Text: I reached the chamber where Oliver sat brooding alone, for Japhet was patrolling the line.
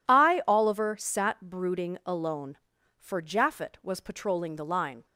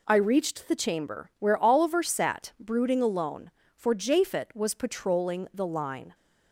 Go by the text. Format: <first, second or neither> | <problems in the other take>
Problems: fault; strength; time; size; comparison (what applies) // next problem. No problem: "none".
second | skips "reached the chamber where"; at 0.4 s